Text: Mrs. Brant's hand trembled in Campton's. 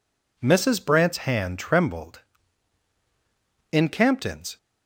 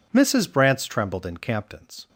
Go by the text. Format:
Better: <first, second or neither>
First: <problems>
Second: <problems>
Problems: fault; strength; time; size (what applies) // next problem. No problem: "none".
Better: first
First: none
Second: skips "hand"; at 0.8 s